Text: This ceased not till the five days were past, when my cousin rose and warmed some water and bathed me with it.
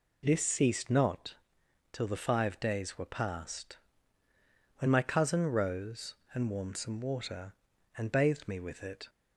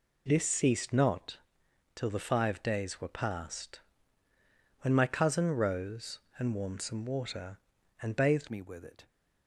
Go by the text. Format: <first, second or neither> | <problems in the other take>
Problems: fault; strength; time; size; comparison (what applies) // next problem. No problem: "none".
first | pauses between "not" and "till"; noticeable; at 1.3 s; 0.58 s long; noticeable in the first // changes voice at "me"; from 8.4 s on; 0.6 s long